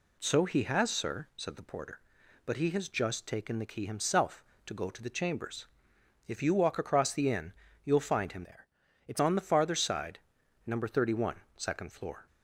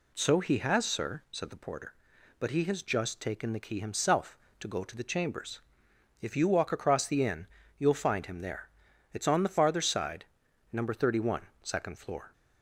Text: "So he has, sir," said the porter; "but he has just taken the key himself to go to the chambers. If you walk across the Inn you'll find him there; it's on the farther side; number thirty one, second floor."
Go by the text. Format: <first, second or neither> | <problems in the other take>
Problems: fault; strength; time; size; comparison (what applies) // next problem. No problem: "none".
second | pauses between "Inn" and "you'll"; slight; at 7.5 s; 0.32 s long; slight in the second // changes voice from "there" to "it's"; from 8.4 to 9.1 s; 0.7 s long